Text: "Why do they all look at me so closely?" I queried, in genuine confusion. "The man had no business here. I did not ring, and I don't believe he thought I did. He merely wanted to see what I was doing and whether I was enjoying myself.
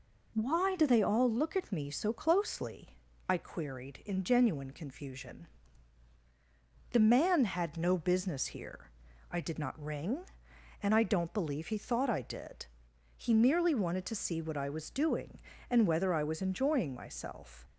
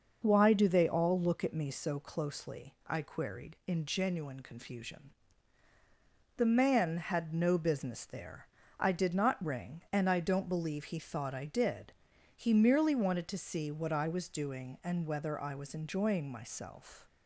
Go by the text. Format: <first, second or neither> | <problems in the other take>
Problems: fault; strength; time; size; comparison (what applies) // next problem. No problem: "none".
first | says "there" for "here"; at 8.0 s